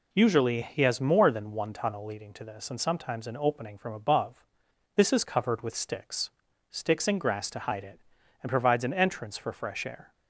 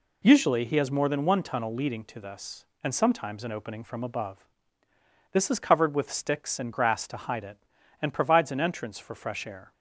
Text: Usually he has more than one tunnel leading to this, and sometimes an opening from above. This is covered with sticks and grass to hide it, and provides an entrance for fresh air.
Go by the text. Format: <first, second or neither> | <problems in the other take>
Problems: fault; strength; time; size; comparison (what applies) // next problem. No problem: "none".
second | says "sticks" twice; at 6.6 s